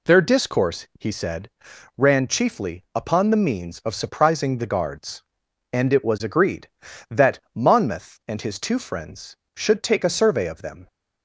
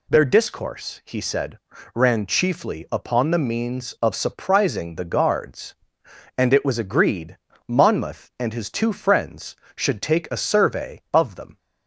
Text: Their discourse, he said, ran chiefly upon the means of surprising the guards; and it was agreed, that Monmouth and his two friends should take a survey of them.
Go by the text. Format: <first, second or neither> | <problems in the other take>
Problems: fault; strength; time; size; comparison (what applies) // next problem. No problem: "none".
first | skips "that"; at 7.5 s